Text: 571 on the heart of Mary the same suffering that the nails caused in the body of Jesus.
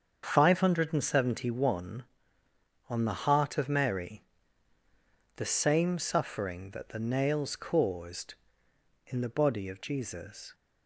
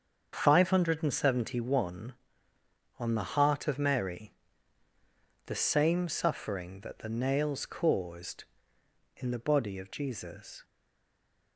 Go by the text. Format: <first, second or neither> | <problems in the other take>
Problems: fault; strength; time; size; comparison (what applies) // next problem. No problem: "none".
first | starts louder than the rest; until 1.4 s; 7 dB; also in the first // pauses between "Mary" and "the"; at 4.3 s; 1.1 s long; also in the first // stays silent after the last word; slight; from 10.6 s on; 0.9 s long